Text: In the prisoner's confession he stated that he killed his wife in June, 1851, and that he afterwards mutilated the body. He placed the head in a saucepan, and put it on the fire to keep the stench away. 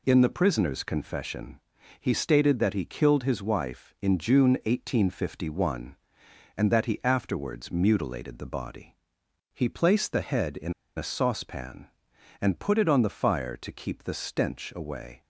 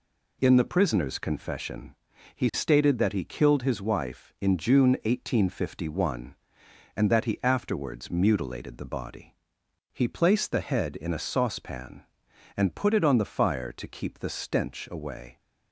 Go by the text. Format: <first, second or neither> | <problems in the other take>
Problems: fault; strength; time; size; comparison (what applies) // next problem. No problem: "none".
second | pauses between "confession" and "he"; at 1.5 s; 0.38 s long; also in the second // pauses between "in" and "a"; slight; at 10.7 s; 0.24 s long